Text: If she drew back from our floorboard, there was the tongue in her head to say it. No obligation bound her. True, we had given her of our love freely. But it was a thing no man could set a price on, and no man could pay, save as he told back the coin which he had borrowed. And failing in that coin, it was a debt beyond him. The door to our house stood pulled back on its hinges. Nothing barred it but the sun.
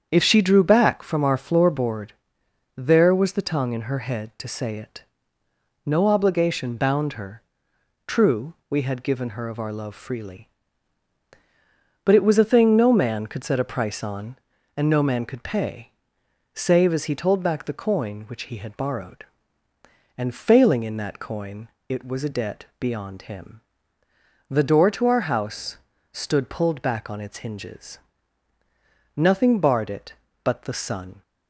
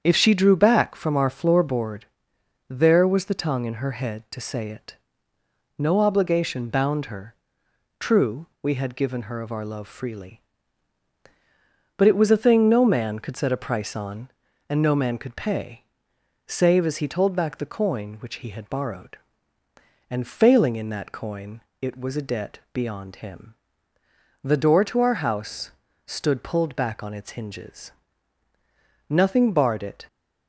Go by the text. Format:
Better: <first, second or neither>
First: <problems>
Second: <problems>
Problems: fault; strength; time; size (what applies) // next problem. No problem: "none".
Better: first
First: starts louder than the rest; strong; until 1.1 s; 8 dB // pauses between "house" and "stood"; slight; at 25.7 s; 0.34 s long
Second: starts louder than the rest; strong; until 1.0 s; 8 dB // pauses between "house" and "stood"; slight; at 25.7 s; 0.34 s long // stops before "but the sun"; at 30.0 s